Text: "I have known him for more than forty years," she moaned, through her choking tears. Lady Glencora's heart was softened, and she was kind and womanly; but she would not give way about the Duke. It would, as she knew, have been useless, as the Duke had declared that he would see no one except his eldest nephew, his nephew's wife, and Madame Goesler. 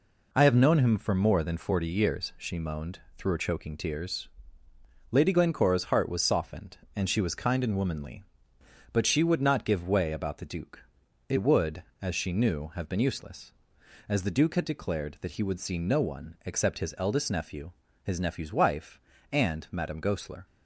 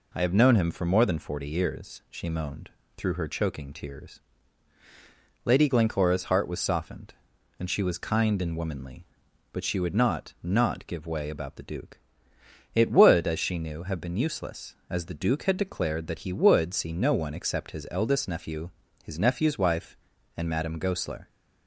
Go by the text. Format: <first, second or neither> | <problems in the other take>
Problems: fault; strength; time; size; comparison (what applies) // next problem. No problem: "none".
first | says "not" twice; at 10.4 s